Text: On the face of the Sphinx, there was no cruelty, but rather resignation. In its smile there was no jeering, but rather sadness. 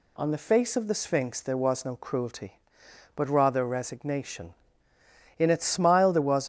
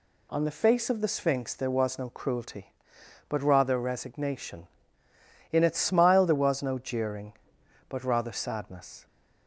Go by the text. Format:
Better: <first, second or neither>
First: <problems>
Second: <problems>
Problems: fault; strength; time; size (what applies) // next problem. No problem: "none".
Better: second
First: stops before "no jeering but rather sadness"; at 6.4 s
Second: none